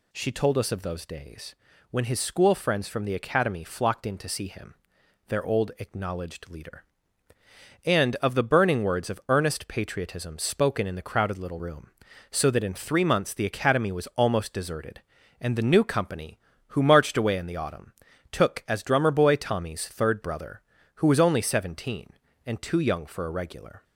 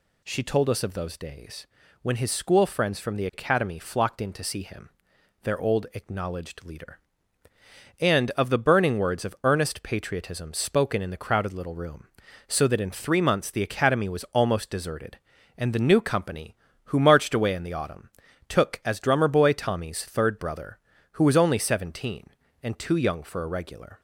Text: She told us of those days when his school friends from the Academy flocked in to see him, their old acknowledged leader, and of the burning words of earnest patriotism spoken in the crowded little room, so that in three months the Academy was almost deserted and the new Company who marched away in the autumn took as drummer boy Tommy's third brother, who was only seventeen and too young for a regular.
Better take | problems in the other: neither | pauses between "days" and "when"; slight; the same in both // pauses between "autumn" and "took"; the same in both

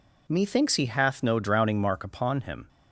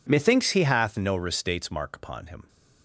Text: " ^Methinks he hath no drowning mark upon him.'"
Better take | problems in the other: first | says "restates" for "drowning"; at 1.1 s

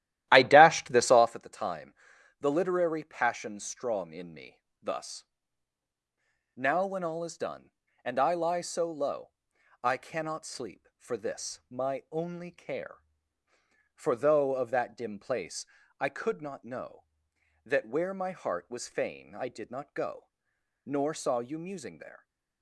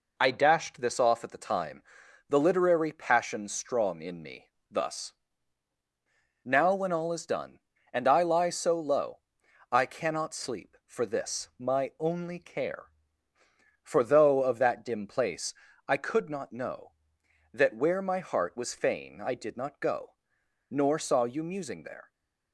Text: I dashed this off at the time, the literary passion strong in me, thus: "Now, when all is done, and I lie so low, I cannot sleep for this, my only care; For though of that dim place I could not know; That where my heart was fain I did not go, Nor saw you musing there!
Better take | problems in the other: second | starts louder than the rest; strong; until 1.4 s; 13.5 dB // pauses between "place" and "I"; slight; at 15.6 s; 0.34 s long; slight in the second

